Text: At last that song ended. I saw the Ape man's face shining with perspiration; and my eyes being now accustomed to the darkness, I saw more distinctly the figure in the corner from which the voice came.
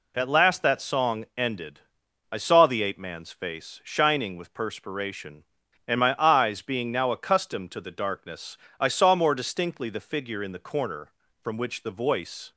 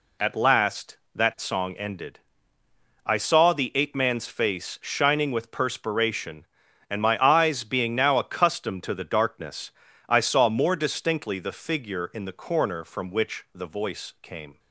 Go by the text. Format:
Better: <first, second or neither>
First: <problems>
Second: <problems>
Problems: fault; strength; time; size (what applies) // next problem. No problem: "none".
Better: second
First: stops before "came"; at 12.5 s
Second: none